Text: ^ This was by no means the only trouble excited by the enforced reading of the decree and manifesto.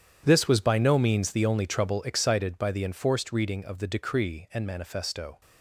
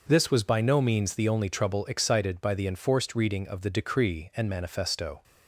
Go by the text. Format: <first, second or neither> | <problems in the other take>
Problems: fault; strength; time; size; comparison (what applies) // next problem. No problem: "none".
second | gets quieter; strong; throughout; 15 dB // starts louder than the rest; strong; until 1.2 s; 9.5 dB; noticeable in the second